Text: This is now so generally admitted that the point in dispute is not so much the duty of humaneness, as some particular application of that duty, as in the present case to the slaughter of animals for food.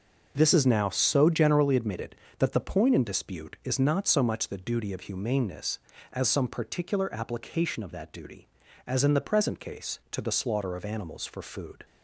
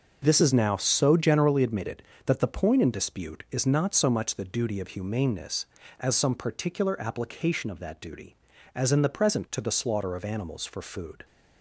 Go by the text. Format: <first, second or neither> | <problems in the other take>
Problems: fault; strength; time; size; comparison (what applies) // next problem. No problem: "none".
first | skips "case"; at 9.4 s